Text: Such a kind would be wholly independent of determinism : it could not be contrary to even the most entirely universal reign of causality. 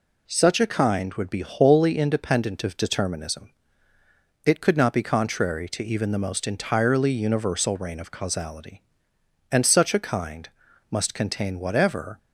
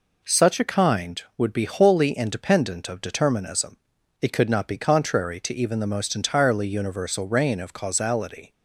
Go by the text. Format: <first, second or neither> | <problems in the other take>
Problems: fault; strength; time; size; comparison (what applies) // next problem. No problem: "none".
second | goes on to say "And such a kind must contain whatever"; strong; from 9.5 s on; 2.6 s long